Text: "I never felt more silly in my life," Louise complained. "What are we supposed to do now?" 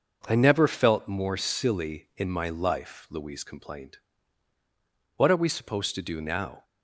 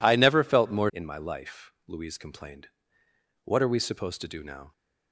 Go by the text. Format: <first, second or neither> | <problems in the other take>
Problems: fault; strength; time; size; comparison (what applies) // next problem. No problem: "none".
first | skips "silly"; at 0.8 s